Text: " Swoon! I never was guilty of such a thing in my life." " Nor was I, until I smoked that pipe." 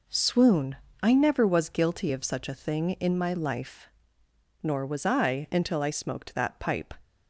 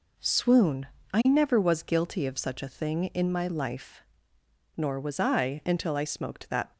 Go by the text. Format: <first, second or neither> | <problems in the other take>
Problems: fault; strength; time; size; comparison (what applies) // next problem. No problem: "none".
first | stops before "pipe"; at 6.7 s